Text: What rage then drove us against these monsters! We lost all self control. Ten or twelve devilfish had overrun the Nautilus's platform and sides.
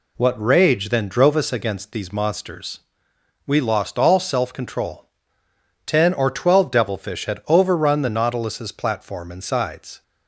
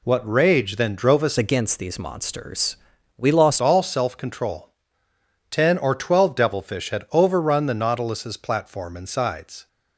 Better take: first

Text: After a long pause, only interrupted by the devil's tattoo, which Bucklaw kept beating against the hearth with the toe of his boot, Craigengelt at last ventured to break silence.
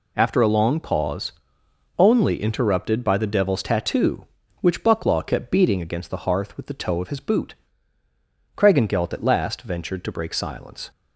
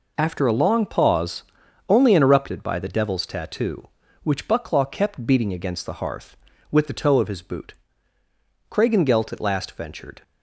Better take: first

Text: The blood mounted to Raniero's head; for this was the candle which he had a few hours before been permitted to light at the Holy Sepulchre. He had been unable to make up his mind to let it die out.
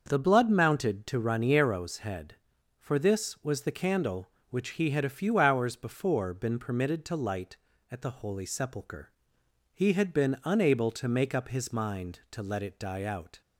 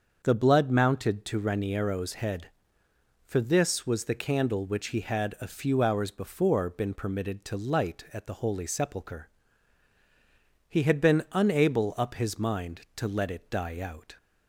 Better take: first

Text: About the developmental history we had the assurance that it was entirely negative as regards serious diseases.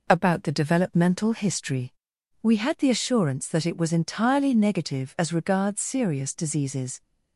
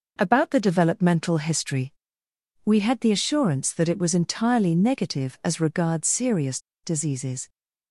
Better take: first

